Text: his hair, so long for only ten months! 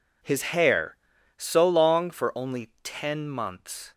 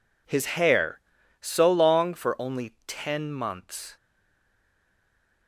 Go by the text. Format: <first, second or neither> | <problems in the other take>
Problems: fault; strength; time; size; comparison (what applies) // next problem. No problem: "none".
first | stays silent after the last word; noticeable; from 3.9 s on; 1.5 s long